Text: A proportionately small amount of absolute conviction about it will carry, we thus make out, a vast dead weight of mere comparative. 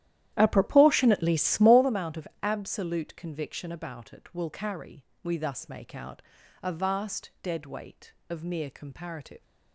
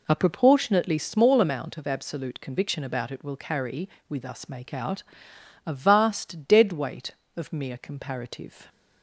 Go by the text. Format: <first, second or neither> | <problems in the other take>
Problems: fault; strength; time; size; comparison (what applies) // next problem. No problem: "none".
second | starts louder than the rest; strong; until 1.8 s; 12.5 dB